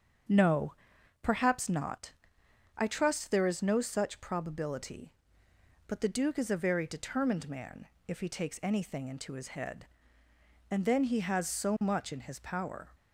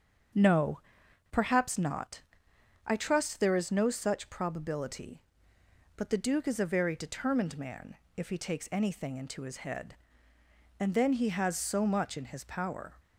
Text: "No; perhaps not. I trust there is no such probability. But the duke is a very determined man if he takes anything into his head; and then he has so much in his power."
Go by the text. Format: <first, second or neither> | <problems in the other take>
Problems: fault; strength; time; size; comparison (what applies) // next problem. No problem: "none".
neither | starts louder than the rest; strong; the same in both // pauses between "man" and "if"; slight; the same in both